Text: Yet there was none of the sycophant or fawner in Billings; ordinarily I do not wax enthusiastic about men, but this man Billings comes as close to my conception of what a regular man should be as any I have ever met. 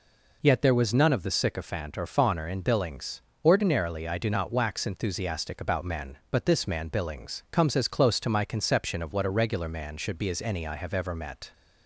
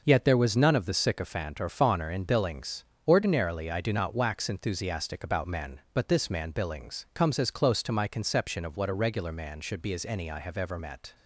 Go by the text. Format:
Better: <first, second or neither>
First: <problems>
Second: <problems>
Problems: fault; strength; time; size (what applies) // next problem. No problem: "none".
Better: first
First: none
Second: gets quieter; strong; throughout; 7 dB